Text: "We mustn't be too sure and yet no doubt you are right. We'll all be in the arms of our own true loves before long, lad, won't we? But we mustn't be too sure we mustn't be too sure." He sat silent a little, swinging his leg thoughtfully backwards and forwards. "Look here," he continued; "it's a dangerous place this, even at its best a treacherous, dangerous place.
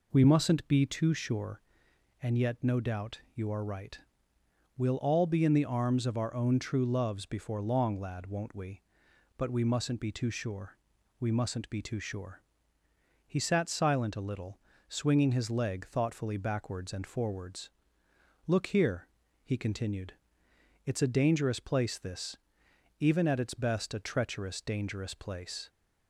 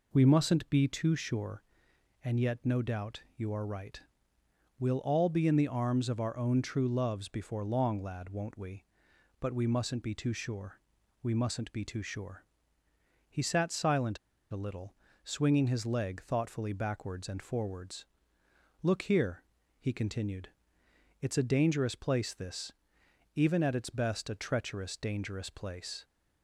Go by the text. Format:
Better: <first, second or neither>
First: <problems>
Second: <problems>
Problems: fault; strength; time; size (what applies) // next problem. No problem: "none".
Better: first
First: pauses between "sure" and "we"; noticeable; at 10.7 s; 0.46 s long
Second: pauses between "sure" and "we"; noticeable; at 10.7 s; 0.46 s long // pauses between "silent" and "a"; slight; at 14.1 s; 0.33 s long